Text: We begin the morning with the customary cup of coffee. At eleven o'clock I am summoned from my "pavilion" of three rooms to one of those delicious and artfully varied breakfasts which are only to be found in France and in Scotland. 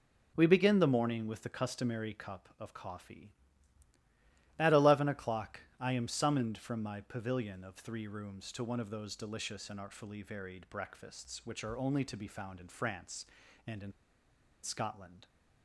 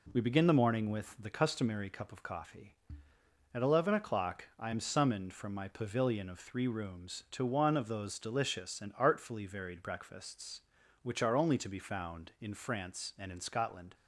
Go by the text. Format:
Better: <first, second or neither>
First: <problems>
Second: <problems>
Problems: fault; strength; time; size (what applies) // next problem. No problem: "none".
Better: second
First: pauses between "o'clock" and "I"; slight; at 5.6 s; 0.18 s long // pauses between "in" and "Scotland"; noticeable; at 13.9 s; 0.71 s long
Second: none